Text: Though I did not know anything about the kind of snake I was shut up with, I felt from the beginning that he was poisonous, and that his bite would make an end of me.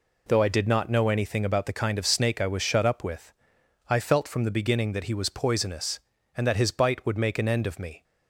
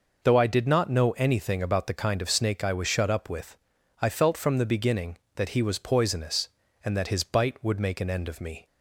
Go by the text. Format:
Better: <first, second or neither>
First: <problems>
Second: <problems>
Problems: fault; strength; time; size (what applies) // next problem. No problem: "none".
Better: neither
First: none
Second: none